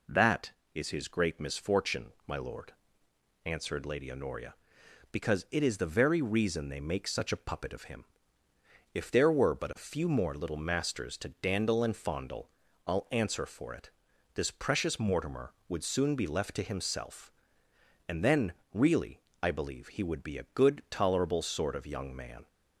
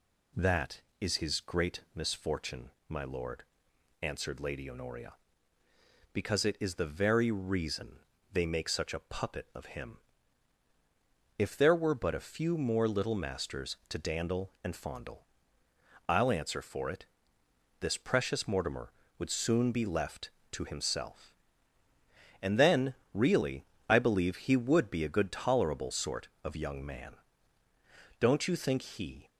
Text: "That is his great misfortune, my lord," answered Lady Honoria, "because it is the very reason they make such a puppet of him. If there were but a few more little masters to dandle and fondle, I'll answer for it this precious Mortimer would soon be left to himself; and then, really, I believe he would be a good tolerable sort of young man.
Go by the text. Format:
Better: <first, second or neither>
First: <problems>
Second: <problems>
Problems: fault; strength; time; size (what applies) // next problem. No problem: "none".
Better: first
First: pauses between "it" and "this"; at 13.9 s; 0.42 s long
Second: pauses between "reason" and "they"; slight; at 7.9 s; 0.32 s long // pauses between "it" and "this"; noticeable; at 17.0 s; 0.76 s long // goes on to say "Don't you think he"; noticeable; from 28.1 s on; 1.1 s long